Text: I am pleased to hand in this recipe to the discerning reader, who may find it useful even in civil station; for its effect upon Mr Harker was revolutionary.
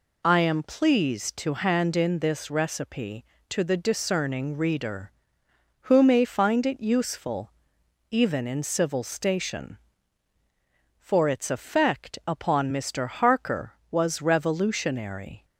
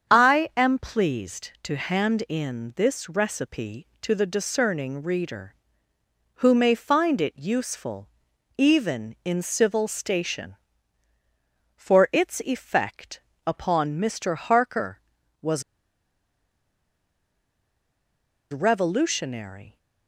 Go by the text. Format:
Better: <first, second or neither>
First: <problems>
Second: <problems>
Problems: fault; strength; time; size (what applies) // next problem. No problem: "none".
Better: first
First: pauses between "useful" and "even"; noticeable; at 7.5 s; 0.58 s long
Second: starts louder than the rest; strong; until 1.1 s; 7.5 dB // pauses between "useful" and "even"; noticeable; at 8.0 s; 0.50 s long // pauses between "effect" and "upon"; slight; at 13.1 s; 0.26 s long // pauses between "was" and "revolutionary"; strong; at 15.6 s; 2.9 s long